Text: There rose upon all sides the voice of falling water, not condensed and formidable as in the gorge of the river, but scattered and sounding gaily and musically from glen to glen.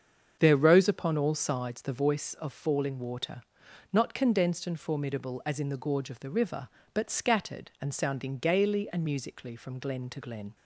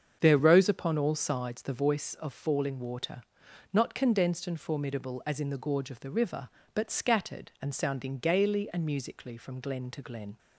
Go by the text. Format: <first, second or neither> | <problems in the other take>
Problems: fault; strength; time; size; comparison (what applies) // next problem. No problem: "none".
neither | starts louder than the rest; the same in both